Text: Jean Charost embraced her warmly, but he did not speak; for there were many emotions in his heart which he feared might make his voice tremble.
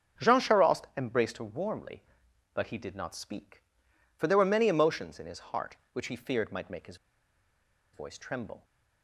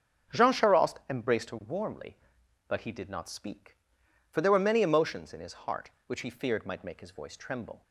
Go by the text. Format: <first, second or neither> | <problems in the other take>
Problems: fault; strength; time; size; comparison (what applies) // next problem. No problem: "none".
second | starts louder than the rest; until 1.3 s; 7 dB; also in the second // pauses between "his" and "voice"; at 6.9 s; 0.98 s long